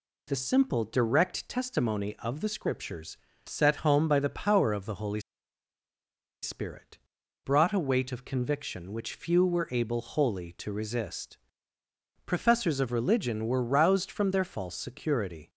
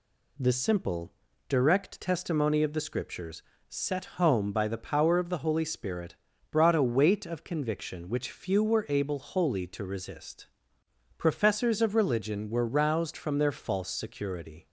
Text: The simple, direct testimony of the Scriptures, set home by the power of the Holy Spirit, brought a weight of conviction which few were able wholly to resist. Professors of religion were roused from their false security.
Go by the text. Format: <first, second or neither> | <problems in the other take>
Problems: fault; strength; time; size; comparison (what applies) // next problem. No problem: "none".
second | pauses between "Holy" and "Spirit"; at 5.2 s; 1.2 s long